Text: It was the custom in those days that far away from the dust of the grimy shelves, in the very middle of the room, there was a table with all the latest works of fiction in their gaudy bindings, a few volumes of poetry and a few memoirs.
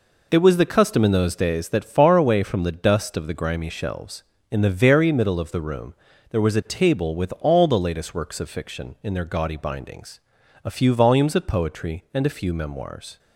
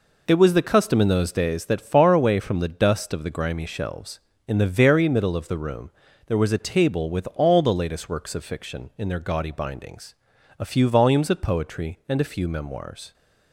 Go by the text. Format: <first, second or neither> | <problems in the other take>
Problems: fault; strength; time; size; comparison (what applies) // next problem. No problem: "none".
neither | none